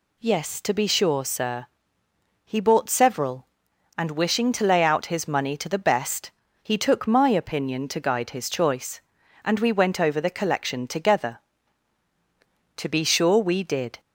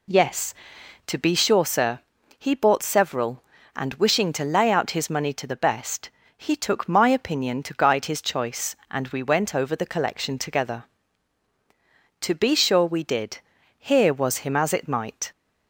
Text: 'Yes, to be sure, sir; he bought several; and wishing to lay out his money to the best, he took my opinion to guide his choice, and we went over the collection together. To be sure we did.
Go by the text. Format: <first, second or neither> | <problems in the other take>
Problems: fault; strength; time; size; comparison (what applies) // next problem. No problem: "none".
first | goes on to say "Here was him as it might"; from 13.7 s on; 1.5 s long